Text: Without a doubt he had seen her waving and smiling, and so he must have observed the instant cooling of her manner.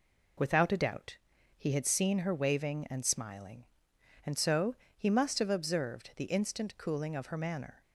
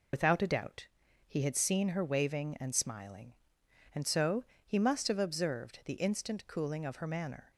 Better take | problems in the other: first | loses the start of "Without"; at 0.1 s; 60 ms // pauses between "doubt" and "he"; at 0.8 s; 0.40 s long; also in the first // pauses between "so" and "he"; slight; at 4.4 s; 0.20 s long; slight in the first

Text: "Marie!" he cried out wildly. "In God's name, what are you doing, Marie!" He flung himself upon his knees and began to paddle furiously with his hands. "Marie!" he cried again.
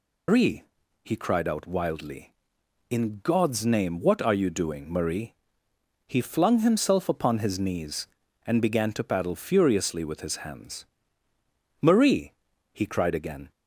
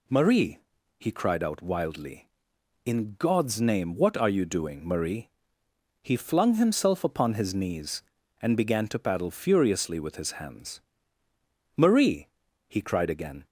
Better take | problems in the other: second | loses the start of "Marie"; at 0.2 s; 155 ms

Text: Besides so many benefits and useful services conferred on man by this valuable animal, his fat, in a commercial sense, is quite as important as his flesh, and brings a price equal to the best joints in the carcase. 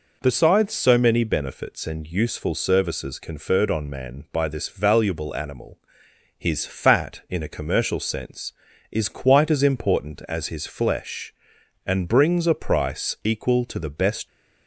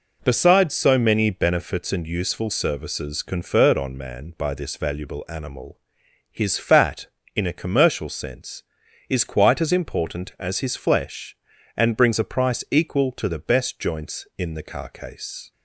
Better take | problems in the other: second | stops before "joints in the carcase"; at 14.2 s

